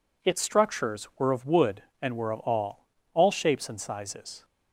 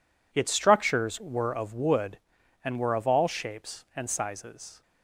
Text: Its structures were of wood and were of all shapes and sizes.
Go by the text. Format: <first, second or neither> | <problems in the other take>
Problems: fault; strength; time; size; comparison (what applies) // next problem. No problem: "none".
second | says "all" twice; at 3.1 s